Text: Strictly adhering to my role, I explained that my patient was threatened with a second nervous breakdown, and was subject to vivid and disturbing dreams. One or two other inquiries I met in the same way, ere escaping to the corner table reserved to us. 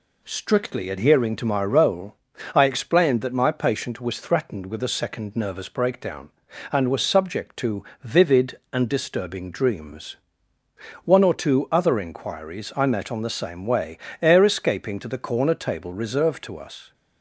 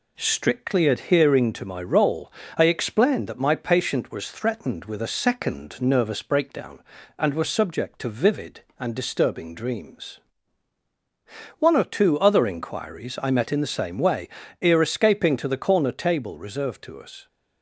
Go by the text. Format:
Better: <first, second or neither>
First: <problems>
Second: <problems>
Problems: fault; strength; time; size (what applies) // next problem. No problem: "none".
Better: second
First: pauses between "to" and "vivid"; slight; at 7.8 s; 0.20 s long // says "on" for "in"; at 13.1 s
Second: none